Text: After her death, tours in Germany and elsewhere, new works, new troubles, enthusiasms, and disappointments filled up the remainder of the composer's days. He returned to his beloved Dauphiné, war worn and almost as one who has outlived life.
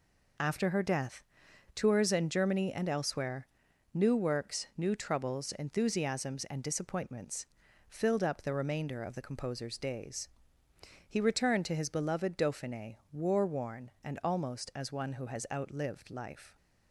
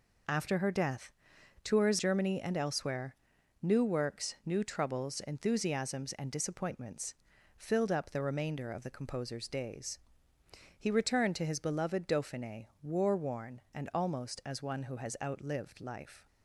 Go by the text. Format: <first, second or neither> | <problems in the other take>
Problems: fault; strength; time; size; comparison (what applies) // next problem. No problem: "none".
first | skips "in"; at 1.9 s // pauses between "disappointments" and "filled"; at 7.1 s; 0.42 s long; also in the first